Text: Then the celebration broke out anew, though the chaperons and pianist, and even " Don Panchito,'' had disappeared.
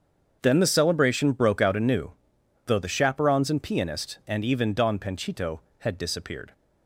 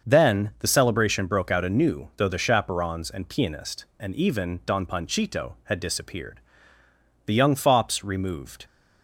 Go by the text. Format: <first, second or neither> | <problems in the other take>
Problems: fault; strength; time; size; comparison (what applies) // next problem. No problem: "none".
first | starts louder than the rest; until 1.1 s; 6.5 dB; also in the first // goes on to say "The young fops removed"; from 7.2 s on; 1.4 s long